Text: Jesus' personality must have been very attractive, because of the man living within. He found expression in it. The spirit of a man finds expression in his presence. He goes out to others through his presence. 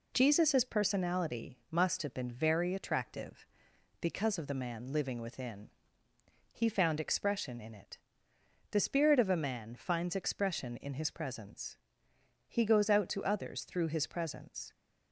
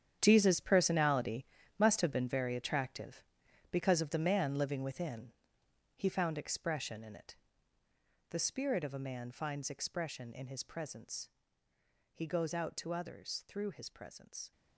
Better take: first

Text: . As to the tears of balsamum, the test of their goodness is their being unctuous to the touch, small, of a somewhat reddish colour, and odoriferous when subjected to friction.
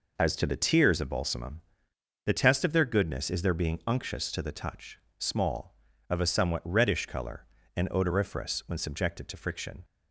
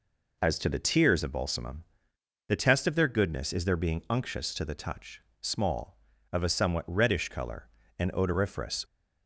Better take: first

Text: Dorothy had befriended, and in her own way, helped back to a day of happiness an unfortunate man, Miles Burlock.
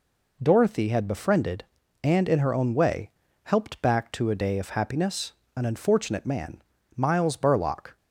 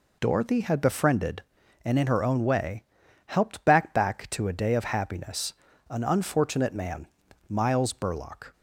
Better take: first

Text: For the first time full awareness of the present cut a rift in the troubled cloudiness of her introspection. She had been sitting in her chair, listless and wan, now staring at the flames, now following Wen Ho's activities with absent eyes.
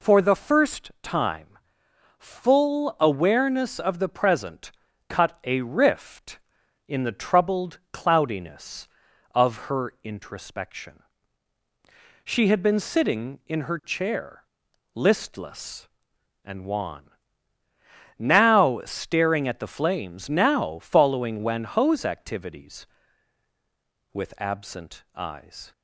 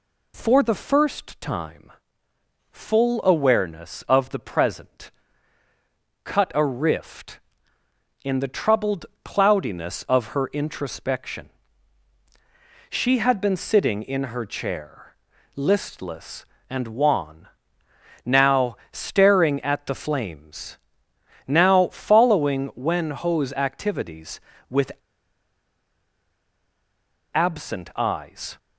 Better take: first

